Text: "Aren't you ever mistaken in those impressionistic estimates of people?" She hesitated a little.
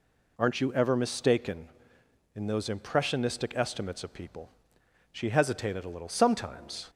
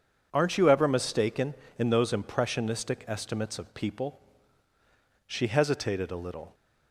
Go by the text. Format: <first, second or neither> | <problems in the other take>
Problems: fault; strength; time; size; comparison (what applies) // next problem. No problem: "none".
second | goes on to say "Sometimes"; noticeable; from 6.0 s on; 0.82 s long